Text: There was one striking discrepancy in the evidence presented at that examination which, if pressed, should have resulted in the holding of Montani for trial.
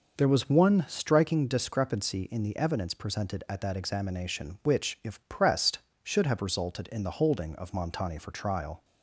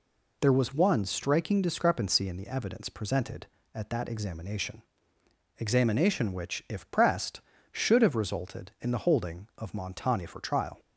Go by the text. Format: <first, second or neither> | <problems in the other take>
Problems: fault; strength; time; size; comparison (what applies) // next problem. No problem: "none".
first | says "examination" twice; at 5.6 s